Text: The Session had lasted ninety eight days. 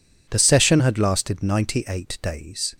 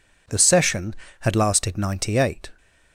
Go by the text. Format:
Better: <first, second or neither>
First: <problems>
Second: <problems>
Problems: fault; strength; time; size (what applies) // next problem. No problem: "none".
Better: first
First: none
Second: stops before "days"; at 2.5 s